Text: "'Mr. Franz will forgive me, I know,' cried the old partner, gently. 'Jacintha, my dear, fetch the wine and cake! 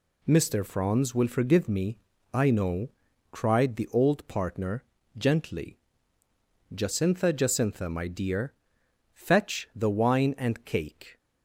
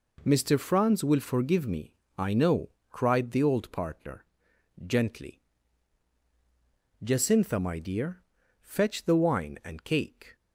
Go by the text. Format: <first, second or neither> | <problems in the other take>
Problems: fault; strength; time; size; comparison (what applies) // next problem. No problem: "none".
second | says "Jacintha" twice; at 7.3 s